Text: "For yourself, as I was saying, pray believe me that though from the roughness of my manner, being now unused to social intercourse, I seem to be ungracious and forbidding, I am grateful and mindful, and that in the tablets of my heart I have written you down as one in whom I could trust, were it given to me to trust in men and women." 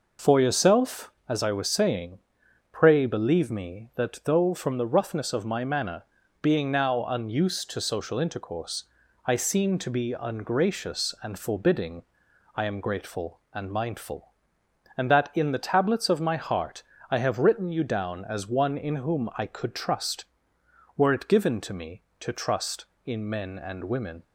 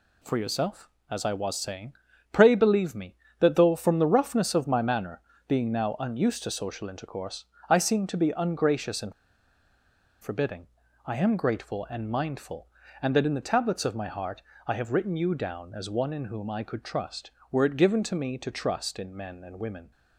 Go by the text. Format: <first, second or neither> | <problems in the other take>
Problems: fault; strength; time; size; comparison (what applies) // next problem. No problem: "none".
first | pauses between "and" and "forbidding"; at 9.1 s; 1.0 s long // pauses between "heart" and "I"; slight; at 14.4 s; 0.24 s long; slight in the first